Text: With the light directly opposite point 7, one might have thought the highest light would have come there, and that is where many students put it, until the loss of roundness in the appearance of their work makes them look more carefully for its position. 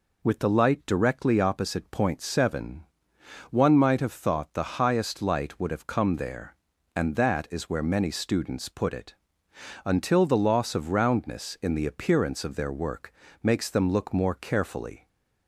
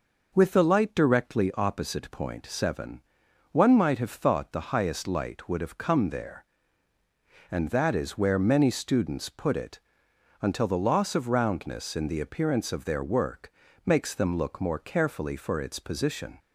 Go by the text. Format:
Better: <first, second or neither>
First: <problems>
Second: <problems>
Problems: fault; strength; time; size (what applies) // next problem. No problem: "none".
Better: second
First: pauses between "work" and "makes"; slight; at 13.1 s; 0.30 s long // stops before "for its position"; at 15.0 s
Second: pauses between "work" and "makes"; slight; at 13.5 s; 0.32 s long